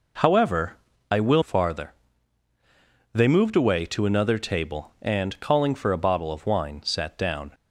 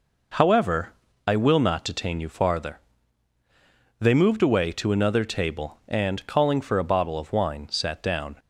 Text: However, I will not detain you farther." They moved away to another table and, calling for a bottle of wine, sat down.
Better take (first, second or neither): second